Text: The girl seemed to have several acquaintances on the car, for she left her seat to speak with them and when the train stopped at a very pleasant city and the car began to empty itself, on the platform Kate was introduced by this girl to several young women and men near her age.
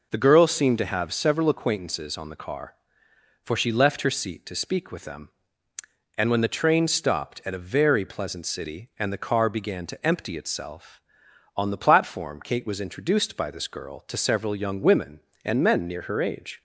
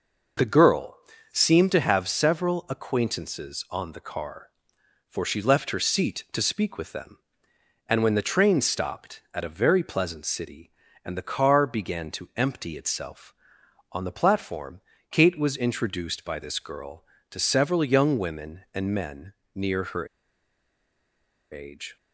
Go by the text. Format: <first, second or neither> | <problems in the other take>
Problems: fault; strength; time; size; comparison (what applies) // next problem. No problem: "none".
first | pauses between "girl" and "seemed"; slight; at 0.9 s; 0.34 s long // pauses between "platform" and "Kate"; slight; at 14.8 s; 0.30 s long // pauses between "men" and "near"; slight; at 19.3 s; 0.24 s long // pauses between "her" and "age"; strong; at 20.0 s; 1.4 s long